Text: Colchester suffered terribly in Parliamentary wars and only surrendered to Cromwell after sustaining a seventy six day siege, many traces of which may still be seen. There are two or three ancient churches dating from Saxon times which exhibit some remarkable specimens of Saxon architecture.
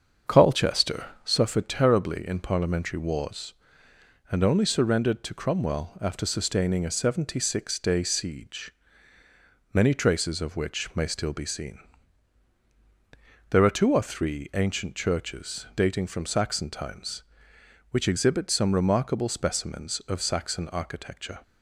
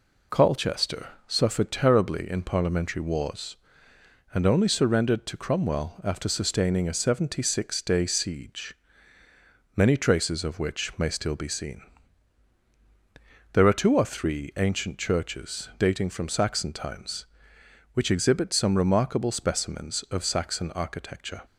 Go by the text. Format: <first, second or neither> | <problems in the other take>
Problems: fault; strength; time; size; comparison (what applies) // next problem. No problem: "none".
second | starts louder than the rest; until 1.5 s; 7 dB // pauses between "Colchester" and "suffered"; slight; at 1.0 s; 0.18 s long; slight in the second